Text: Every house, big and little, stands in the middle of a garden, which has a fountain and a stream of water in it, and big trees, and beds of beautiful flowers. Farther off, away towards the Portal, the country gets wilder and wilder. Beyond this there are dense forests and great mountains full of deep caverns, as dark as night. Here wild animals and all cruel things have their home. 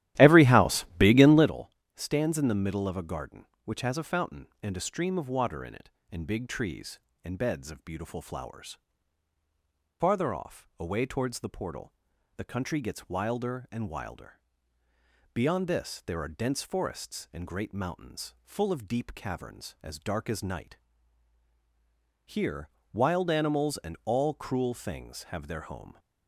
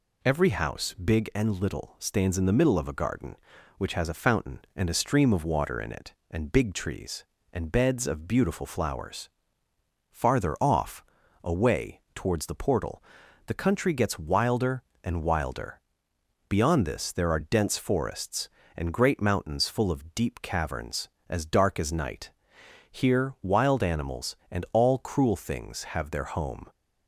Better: second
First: starts louder than the rest; strong; until 1.5 s; 14 dB // pauses between "Here" and "wild"; slight; at 22.6 s; 0.24 s long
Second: none

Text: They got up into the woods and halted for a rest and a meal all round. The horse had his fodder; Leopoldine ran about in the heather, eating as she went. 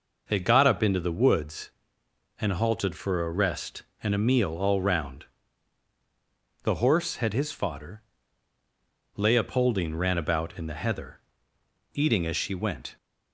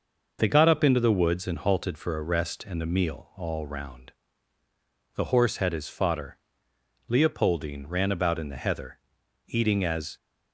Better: first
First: none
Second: stops before "she went"; at 10.1 s

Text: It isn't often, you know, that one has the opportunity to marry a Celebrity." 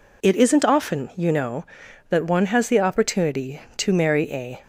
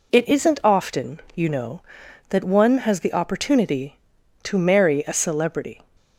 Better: second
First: stops before "Celebrity"; at 4.6 s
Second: none

